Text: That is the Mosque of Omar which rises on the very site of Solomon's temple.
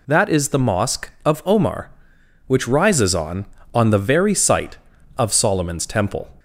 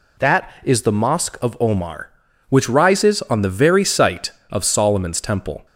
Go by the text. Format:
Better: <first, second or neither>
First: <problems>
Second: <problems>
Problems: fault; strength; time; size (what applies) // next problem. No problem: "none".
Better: second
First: says "on" twice; at 3.7 s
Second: none